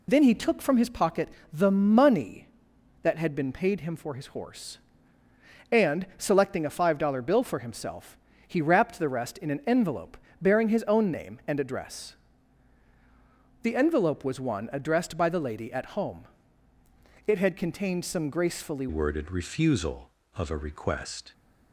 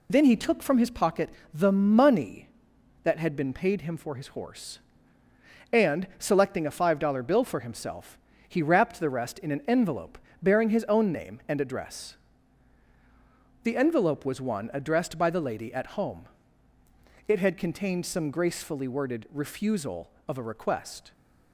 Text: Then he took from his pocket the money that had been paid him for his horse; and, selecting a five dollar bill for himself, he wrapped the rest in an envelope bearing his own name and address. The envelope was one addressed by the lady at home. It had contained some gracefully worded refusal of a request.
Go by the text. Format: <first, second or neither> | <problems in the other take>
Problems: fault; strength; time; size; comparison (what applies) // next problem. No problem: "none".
second | pauses between "pocket" and "the"; slight; at 1.2 s; 0.24 s long; slight in the second // pauses between "envelope" and "bearing"; slight; at 10.1 s; 0.24 s long; slight in the second // changes voice at "worded"; from 18.8 s on; 2.5 s long